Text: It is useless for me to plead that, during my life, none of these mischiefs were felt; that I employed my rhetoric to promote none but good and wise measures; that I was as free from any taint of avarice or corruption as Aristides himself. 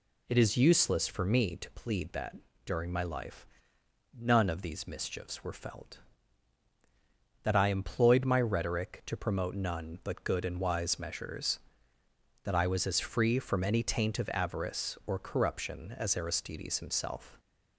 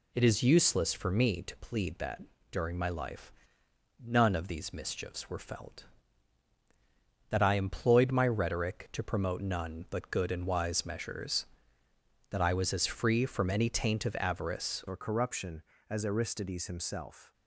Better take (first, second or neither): first